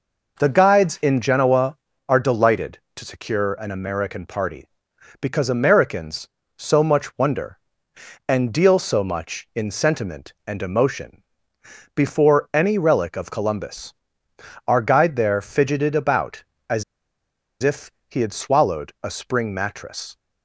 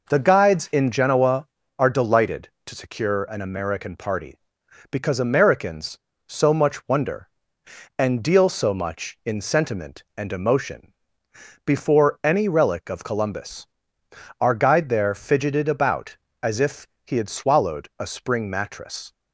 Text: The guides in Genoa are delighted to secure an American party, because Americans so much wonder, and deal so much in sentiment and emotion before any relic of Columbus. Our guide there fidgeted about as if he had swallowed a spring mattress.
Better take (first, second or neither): second